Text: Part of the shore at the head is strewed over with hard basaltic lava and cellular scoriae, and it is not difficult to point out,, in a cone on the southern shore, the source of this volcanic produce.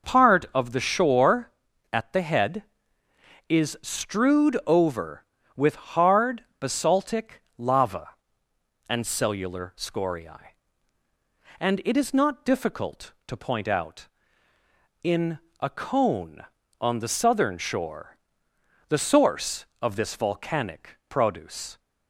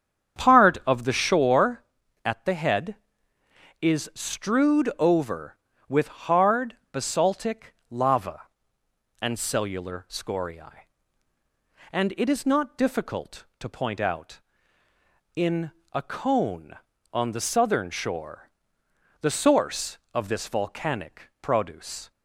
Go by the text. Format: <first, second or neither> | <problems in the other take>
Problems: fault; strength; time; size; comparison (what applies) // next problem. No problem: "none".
first | starts louder than the rest; strong; until 1.4 s; 8 dB // pauses between "basaltic" and "lava"; slight; at 7.7 s; 0.16 s long; slight in the first // pauses between "in" and "a"; slight; at 15.7 s; 0.22 s long; slight in the first